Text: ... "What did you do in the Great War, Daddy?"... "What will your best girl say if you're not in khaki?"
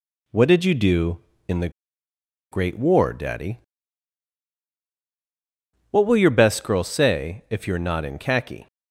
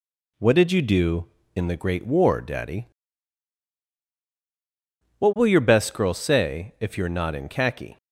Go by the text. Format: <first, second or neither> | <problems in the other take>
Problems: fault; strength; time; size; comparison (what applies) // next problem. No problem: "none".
second | pauses between "the" and "Great"; noticeable; at 1.6 s; 0.82 s long